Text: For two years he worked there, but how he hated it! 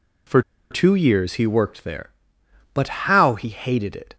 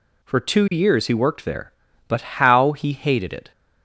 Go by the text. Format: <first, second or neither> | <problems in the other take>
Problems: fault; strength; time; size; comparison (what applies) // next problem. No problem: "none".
second | pauses between "For" and "two"; slight; at 0.4 s; 0.29 s long // pauses between "but" and "how"; slight; at 2.8 s; 0.16 s long